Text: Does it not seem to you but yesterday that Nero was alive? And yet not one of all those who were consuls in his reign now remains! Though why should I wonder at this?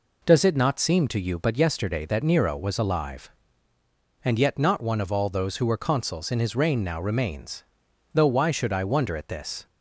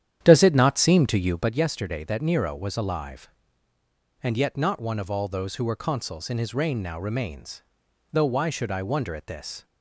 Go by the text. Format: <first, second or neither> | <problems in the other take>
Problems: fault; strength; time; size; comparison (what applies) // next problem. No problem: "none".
first | starts louder than the rest; strong; until 1.6 s; 10 dB